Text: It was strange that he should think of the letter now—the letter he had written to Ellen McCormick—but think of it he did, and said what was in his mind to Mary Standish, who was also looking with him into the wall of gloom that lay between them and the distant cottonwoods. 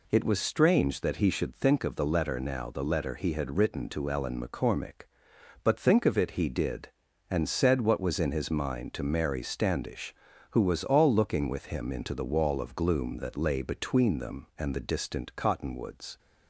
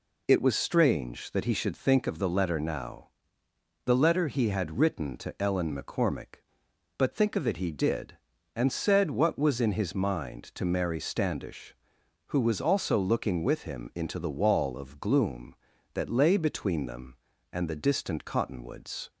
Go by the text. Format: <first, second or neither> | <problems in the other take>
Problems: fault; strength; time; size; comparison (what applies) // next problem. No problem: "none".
second | says "all" for "also"; at 10.8 s